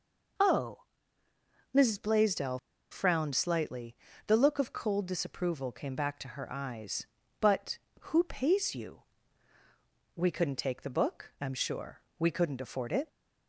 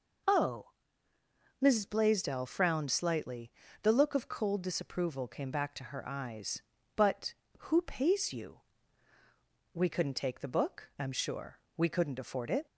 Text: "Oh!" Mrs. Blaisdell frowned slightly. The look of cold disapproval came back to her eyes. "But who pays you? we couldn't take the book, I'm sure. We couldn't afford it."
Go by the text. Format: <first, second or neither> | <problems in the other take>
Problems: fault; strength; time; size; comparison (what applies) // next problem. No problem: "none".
second | pauses between "Blaisdell" and "frowned"; slight; at 2.5 s; 0.33 s long